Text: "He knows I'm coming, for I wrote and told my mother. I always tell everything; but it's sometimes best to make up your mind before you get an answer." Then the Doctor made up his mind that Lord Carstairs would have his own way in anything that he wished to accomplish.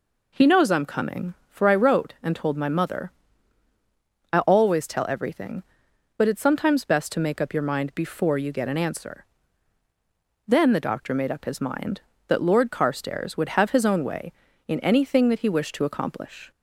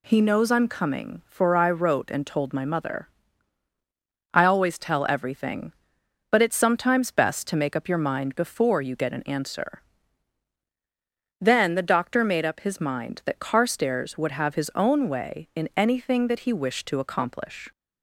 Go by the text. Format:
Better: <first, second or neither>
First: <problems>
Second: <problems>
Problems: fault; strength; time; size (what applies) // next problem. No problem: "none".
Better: first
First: none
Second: skips "Lord"; at 13.3 s